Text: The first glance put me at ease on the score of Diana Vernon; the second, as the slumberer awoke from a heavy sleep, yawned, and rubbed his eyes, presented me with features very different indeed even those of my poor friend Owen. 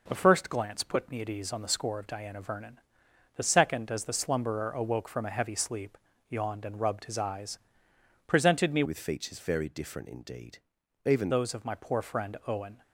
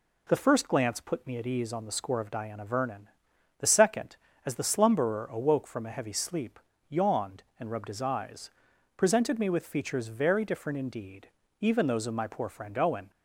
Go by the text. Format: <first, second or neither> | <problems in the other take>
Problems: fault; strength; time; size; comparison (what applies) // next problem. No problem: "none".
second | changes voice from "with" to "even"; from 8.8 to 11.3 s; 2.5 s long // pauses between "indeed" and "even"; noticeable; at 10.5 s; 0.46 s long; slight in the second